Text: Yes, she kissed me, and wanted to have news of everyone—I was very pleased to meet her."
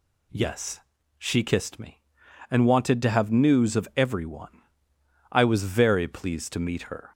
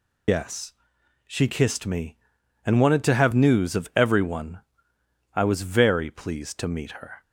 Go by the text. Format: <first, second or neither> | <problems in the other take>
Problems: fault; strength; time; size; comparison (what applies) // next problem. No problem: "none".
first | loses the start of "Yes"; at 0.2 s; 150 ms